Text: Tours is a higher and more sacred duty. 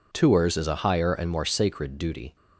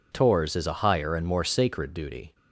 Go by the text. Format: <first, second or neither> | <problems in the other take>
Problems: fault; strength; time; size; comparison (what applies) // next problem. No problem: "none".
neither | none